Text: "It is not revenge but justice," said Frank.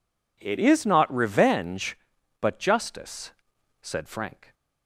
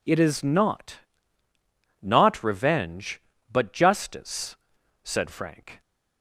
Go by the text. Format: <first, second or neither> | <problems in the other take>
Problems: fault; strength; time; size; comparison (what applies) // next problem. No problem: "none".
first | says "not" twice; at 2.0 s